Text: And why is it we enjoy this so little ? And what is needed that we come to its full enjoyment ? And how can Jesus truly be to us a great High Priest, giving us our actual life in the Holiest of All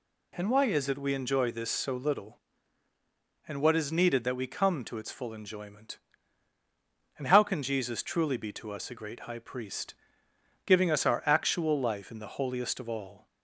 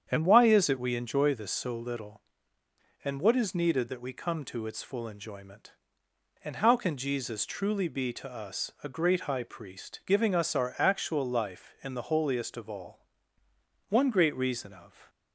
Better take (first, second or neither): first